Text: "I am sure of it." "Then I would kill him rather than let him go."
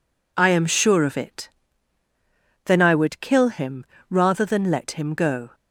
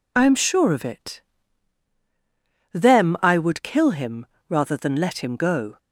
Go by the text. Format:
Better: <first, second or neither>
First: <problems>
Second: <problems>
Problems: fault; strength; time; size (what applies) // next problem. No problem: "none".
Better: first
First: pauses between "him" and "rather"; slight; at 3.8 s; 0.24 s long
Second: says "Them" for "Then"; at 2.7 s // pauses between "him" and "rather"; slight; at 4.2 s; 0.22 s long